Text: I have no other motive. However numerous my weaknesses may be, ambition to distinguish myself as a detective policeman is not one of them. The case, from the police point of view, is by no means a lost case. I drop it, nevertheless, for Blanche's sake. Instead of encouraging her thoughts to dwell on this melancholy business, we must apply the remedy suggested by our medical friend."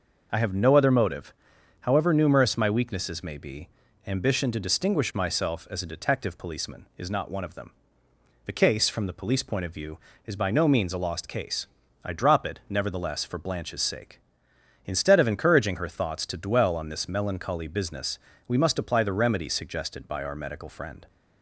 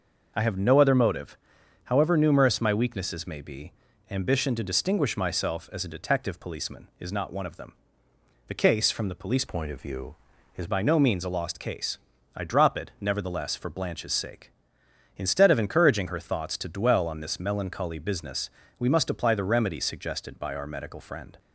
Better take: first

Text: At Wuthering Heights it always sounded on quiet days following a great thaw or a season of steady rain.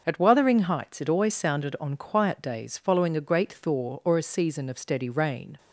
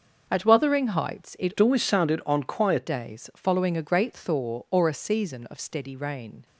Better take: first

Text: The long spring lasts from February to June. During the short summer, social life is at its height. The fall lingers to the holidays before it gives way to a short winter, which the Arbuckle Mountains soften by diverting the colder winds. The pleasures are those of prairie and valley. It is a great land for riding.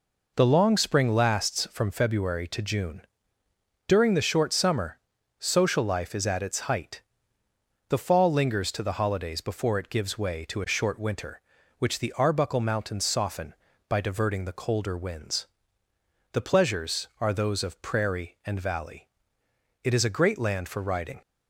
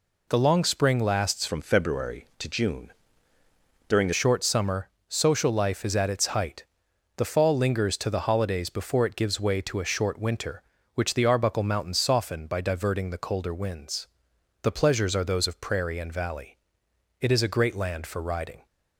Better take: first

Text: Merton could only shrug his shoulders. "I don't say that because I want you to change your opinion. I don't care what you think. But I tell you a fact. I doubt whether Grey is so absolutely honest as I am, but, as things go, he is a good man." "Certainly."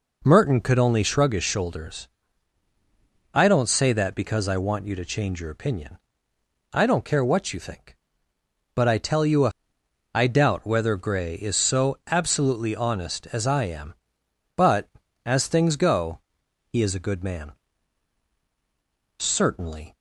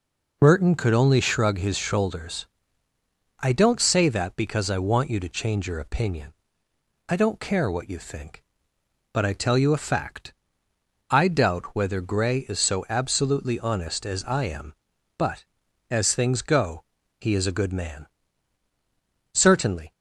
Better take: second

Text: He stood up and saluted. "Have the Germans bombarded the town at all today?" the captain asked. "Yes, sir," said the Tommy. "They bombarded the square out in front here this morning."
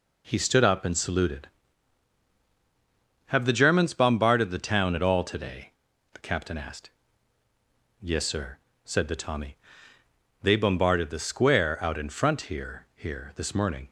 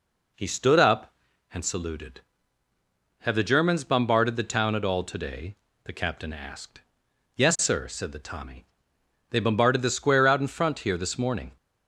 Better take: second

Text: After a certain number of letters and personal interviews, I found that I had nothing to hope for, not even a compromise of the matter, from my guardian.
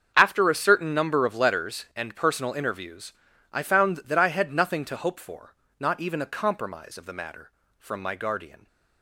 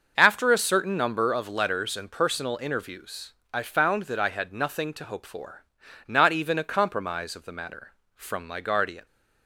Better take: neither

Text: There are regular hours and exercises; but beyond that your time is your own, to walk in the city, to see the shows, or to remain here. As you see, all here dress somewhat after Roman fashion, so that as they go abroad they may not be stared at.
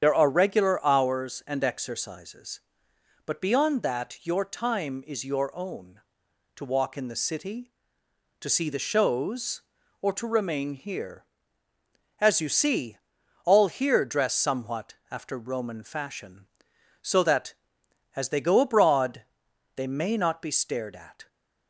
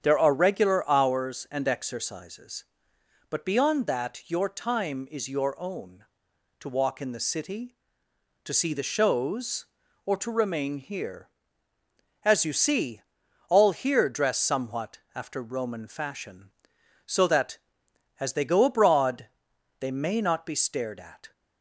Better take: second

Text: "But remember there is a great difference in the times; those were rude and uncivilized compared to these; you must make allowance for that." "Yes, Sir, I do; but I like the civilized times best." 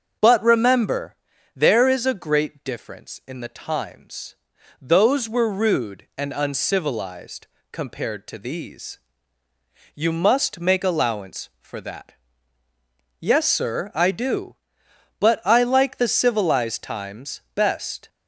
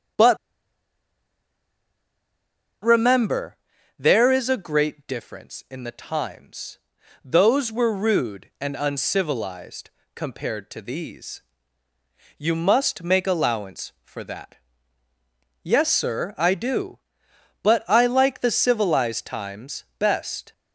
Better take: first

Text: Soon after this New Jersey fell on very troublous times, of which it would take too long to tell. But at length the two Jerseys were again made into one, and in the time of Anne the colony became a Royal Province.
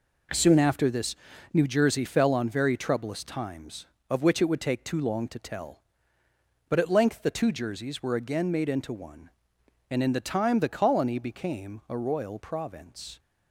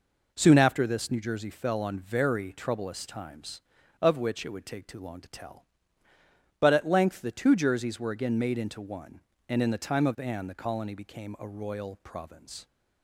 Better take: second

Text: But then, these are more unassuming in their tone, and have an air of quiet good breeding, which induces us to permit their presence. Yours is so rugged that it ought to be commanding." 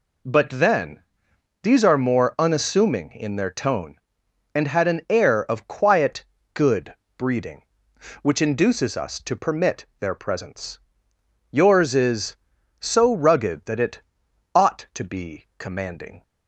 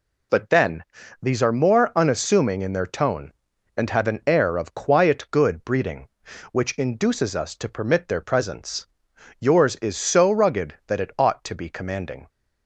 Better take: second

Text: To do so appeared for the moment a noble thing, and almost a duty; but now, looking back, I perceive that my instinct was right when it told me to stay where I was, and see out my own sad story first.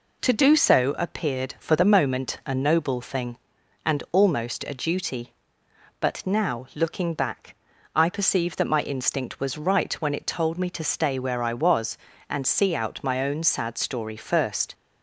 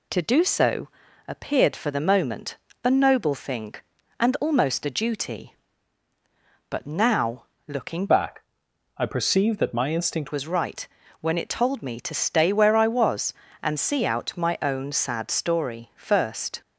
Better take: first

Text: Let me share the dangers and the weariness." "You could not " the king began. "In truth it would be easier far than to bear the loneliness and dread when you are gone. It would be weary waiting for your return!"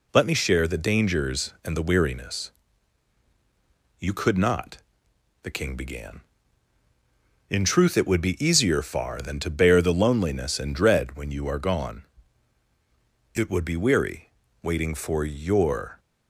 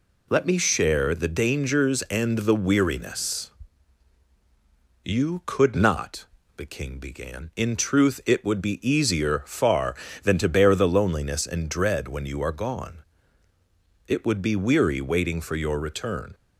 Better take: second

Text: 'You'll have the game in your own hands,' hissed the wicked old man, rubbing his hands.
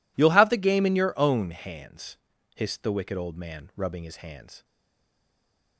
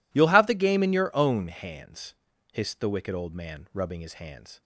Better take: second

